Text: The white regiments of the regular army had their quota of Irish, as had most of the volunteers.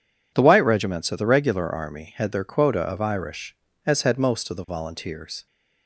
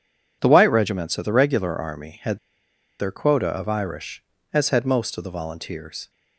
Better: first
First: none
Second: pauses between "had" and "their"; noticeable; at 2.3 s; 0.62 s long

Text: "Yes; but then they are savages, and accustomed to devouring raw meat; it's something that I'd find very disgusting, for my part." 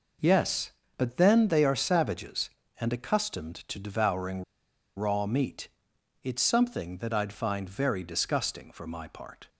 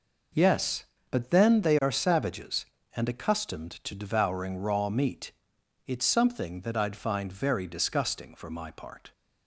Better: second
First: pauses between "devouring" and "raw"; noticeable; at 4.4 s; 0.54 s long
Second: none

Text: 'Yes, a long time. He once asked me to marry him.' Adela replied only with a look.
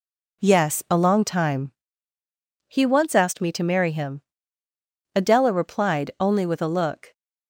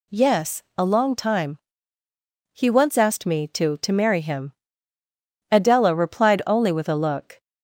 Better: first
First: none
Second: says "to" twice; at 3.7 s

